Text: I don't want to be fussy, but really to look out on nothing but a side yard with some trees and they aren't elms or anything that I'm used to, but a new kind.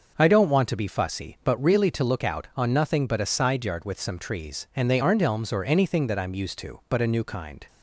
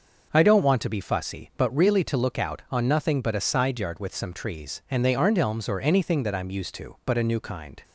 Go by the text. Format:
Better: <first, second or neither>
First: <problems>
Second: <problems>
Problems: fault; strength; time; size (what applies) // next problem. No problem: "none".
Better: neither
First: starts louder than the rest; noticeable; until 1.1 s; 6 dB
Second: starts louder than the rest; until 1.3 s; 6 dB